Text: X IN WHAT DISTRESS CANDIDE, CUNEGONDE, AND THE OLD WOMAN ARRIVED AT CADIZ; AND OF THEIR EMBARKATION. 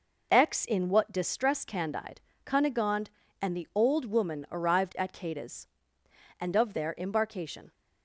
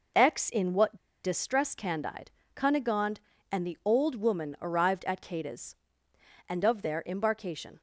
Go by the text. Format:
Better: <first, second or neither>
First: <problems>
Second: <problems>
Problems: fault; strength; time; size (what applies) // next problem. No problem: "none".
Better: first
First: none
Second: pauses between "WHAT" and "DISTRESS"; slight; at 0.9 s; 0.27 s long